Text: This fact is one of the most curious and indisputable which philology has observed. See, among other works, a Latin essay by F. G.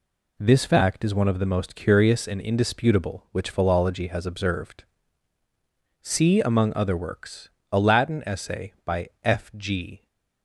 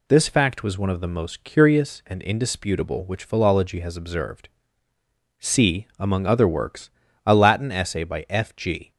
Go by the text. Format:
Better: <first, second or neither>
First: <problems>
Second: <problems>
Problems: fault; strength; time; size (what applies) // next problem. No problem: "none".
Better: first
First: none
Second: says "was" for "is"; at 0.6 s